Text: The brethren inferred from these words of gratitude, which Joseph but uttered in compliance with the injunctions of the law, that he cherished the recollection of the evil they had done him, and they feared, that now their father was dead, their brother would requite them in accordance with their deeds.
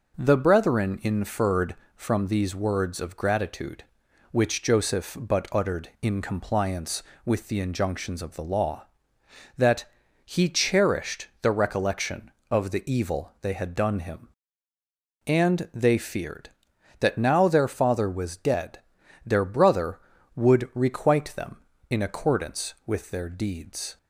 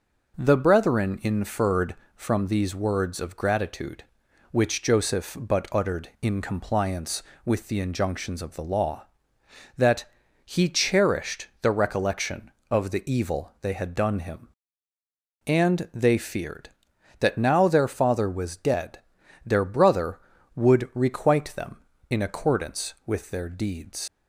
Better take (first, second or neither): first